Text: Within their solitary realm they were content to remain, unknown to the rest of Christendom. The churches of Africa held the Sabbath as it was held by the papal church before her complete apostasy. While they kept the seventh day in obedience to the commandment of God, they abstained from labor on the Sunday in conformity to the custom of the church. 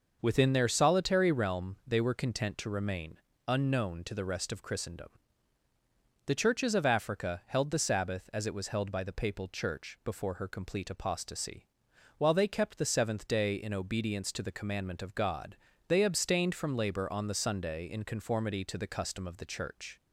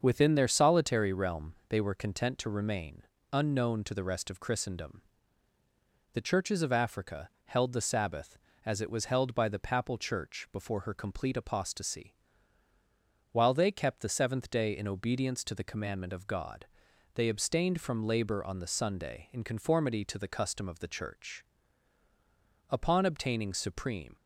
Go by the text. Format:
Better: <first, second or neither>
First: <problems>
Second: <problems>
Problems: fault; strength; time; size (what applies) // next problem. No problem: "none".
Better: first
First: starts louder than the rest; noticeable; until 1.2 s; 6 dB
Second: starts louder than the rest; until 1.0 s; 7 dB // pauses between "realm" and "they"; slight; at 1.5 s; 0.16 s long // goes on to say "Upon obtaining supreme"; from 22.6 s on; 1.4 s long